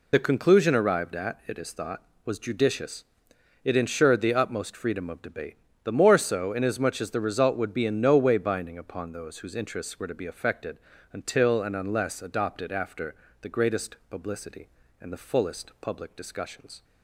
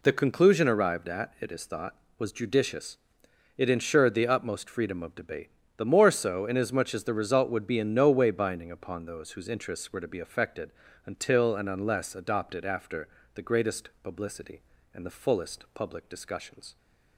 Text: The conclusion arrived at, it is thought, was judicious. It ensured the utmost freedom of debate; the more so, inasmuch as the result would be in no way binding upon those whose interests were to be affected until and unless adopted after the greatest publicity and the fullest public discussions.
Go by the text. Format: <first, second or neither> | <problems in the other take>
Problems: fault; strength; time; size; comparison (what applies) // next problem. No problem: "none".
second | loses the start of "The"; at 0.1 s; 35 ms // pauses between "affected" and "until"; slight; at 10.7 s; 0.34 s long; slight in the second // pauses between "after" and "the"; slight; at 13.1 s; 0.26 s long; slight in the second